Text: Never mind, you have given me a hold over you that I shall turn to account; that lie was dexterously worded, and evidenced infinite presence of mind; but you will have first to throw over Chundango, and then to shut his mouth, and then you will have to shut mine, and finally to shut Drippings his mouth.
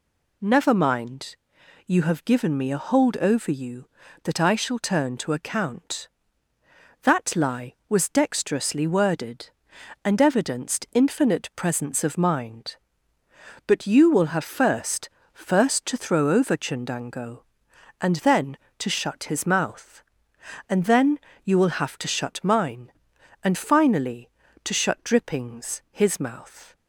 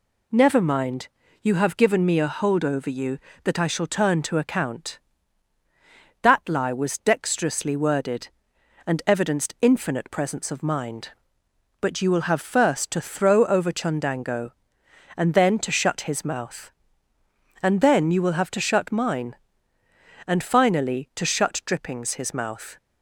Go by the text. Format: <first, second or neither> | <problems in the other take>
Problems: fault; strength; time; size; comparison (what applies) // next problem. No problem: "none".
second | says "first" twice; at 15.3 s // pauses between "then" and "you"; slight; at 21.1 s; 0.28 s long